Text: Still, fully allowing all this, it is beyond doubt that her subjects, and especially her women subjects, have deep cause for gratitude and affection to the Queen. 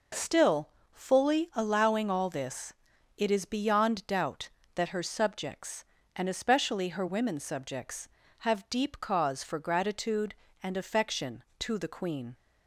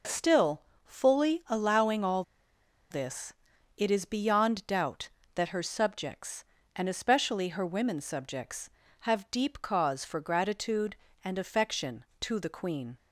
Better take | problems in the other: first | pauses between "all" and "this"; noticeable; at 2.2 s; 0.68 s long

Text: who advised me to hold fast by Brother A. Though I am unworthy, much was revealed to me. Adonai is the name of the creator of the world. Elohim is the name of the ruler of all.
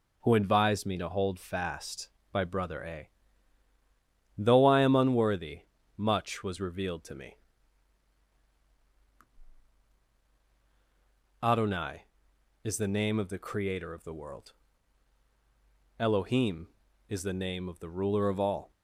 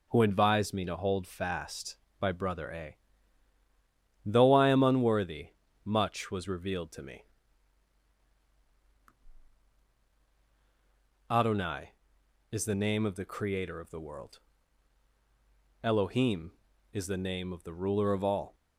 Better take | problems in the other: neither | none

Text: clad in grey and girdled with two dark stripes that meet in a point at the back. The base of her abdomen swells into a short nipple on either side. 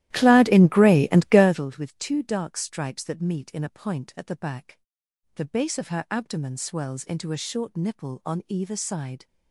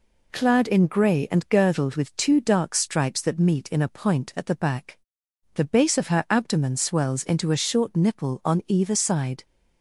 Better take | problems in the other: second | starts louder than the rest; strong; until 1.6 s; 14 dB

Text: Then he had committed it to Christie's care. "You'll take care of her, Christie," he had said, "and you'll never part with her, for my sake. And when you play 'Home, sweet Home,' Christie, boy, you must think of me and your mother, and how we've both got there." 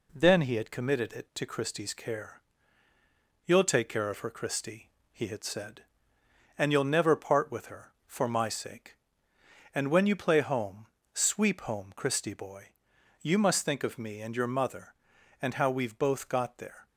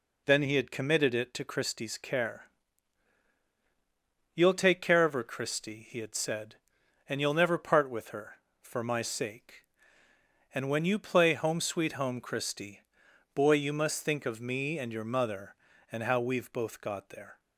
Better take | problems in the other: second | says "sweep" for "sweet"; at 11.1 s

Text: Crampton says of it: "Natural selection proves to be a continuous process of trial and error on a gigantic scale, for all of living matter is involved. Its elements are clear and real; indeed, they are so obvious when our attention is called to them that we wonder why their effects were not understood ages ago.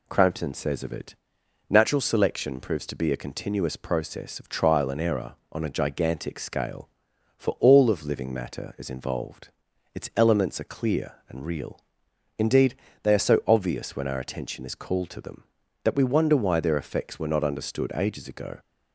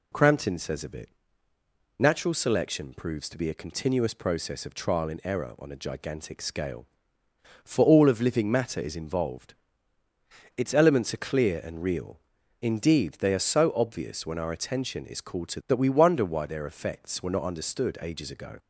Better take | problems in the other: first | skips "them"; at 15.6 s

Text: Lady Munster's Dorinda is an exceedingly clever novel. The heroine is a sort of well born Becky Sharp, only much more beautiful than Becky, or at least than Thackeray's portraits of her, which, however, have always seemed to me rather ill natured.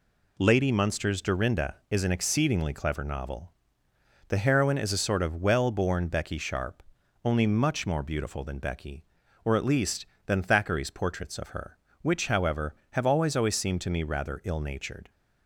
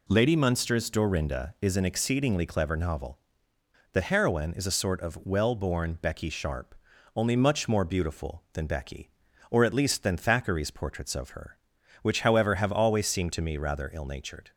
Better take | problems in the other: second | says "always" twice; at 13.3 s

